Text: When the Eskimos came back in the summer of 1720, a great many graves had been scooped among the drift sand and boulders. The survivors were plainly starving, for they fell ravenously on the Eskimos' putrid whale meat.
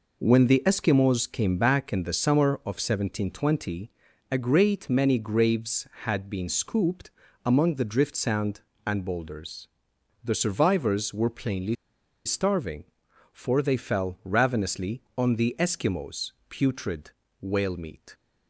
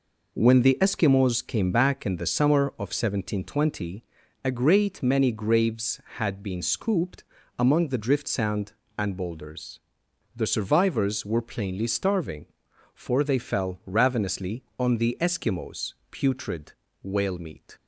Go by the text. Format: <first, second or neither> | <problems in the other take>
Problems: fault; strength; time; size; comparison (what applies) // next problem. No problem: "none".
second | pauses between "scooped" and "among"; slight; at 7.0 s; 0.36 s long; slight in the second // pauses between "plainly" and "starving"; noticeable; at 11.7 s; 0.51 s long // pauses between "Eskimos" and "putrid"; slight; at 16.2 s; 0.20 s long; slight in the second // pauses between "putrid" and "whale"; slight; at 17.0 s; 0.30 s long; slight in the second